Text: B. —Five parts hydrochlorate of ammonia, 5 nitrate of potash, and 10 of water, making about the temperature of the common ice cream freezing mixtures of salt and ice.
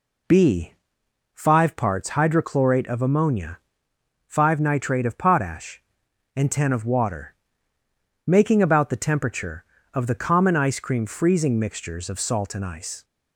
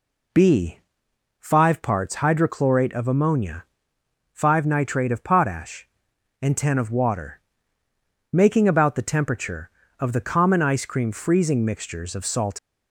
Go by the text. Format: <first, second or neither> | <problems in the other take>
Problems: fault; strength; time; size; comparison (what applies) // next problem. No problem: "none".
first | stops before "and ice"; at 12.5 s